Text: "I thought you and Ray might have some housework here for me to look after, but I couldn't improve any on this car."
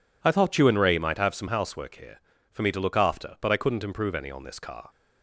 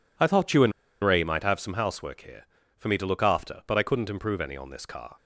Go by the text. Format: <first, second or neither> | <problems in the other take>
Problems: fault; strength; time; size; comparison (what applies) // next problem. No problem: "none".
first | pauses between "and" and "Ray"; slight; at 0.7 s; 0.32 s long